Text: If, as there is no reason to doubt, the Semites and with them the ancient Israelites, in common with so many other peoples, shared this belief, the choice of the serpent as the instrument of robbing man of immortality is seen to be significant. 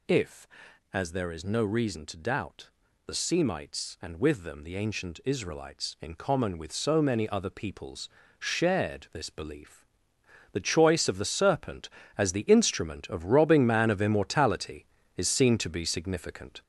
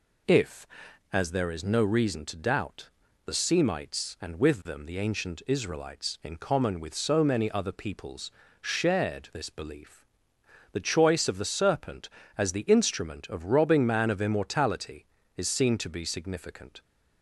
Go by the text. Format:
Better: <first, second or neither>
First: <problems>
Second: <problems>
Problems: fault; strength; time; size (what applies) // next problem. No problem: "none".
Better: second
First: gets louder; noticeable; throughout; 4.5 dB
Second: none